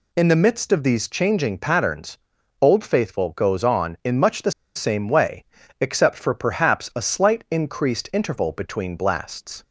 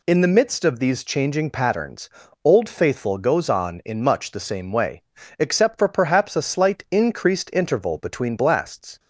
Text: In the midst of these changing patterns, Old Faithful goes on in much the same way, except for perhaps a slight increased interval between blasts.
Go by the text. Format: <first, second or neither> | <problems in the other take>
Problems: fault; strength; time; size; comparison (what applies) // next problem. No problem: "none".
second | pauses between "the" and "same"; slight; at 4.5 s; 0.25 s long